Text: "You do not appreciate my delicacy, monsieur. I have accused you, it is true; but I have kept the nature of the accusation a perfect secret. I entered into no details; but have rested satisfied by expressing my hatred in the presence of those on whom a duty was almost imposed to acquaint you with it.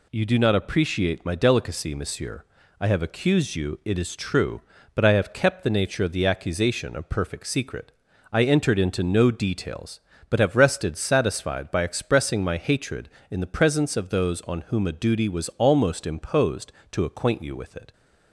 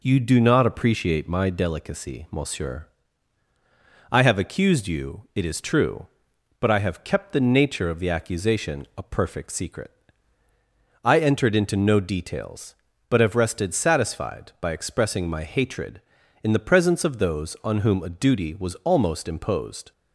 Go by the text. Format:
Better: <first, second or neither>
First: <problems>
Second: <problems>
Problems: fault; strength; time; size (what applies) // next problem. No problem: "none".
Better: first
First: none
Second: stops before "to acquaint you with it"; at 19.9 s